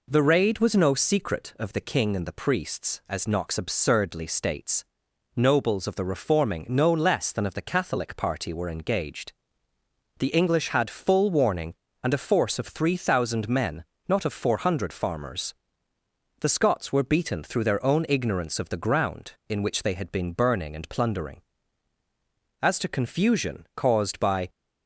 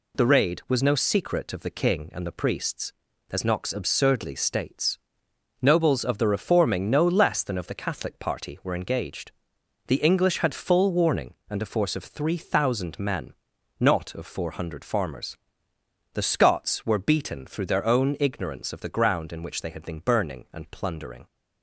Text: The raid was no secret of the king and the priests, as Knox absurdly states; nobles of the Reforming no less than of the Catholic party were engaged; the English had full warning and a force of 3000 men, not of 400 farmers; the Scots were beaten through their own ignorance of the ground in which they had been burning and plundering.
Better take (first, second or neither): second